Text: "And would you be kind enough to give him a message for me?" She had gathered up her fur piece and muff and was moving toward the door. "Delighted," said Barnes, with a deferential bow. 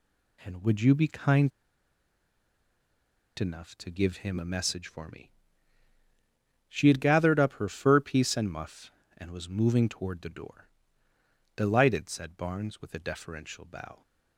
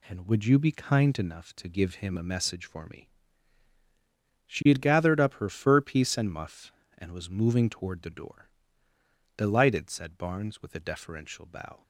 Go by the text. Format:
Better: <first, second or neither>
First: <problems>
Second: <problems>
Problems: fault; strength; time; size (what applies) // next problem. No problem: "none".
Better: second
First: pauses between "kind" and "enough"; strong; at 1.5 s; 1.8 s long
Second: none